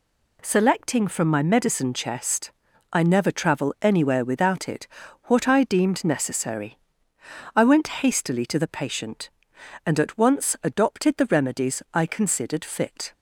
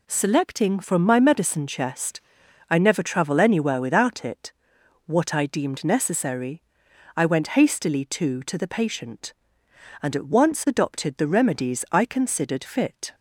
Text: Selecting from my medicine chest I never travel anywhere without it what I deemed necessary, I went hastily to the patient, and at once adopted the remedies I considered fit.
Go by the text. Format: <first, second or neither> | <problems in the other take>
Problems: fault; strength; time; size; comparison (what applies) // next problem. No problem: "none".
first | pauses between "chest" and "I"; noticeable; at 2.2 s; 0.48 s long; also in the first // pauses between "it" and "what"; noticeable; at 4.5 s; 0.54 s long; also in the first // says "to" twice; at 8.4 s